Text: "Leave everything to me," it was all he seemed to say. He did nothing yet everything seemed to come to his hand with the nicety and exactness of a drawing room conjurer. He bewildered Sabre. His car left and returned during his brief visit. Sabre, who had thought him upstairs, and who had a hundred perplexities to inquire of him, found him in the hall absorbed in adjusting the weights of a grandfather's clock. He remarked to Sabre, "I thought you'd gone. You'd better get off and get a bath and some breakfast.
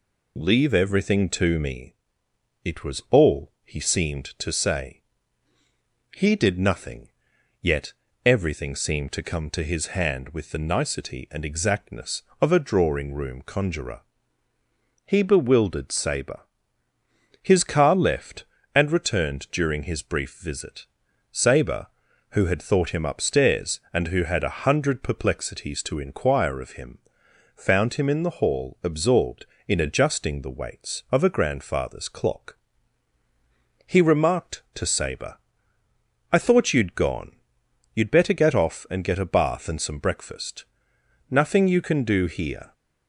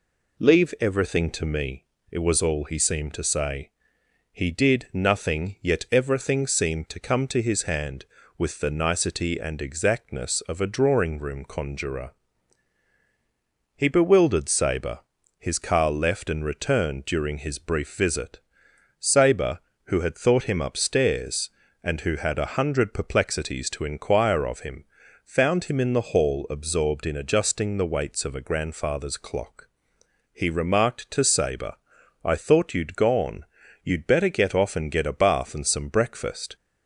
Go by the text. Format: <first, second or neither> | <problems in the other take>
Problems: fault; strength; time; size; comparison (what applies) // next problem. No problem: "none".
second | pauses between "nothing" and "yet"; noticeable; at 7.0 s; 0.52 s long // pauses between "yet" and "everything"; slight; at 7.9 s; 0.30 s long // goes on to say "Nothing you can do here"; from 41.3 s on; 1.4 s long